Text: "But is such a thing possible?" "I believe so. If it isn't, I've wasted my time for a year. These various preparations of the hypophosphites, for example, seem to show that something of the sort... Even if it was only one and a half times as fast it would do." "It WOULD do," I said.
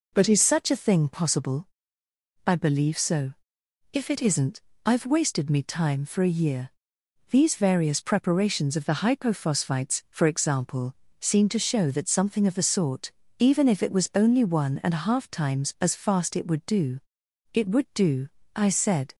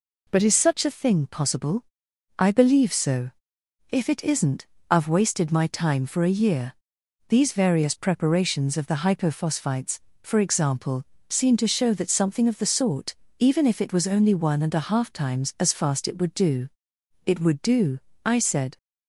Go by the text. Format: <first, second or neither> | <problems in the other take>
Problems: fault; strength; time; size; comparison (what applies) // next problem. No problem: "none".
second | says "me" for "my"; at 5.4 s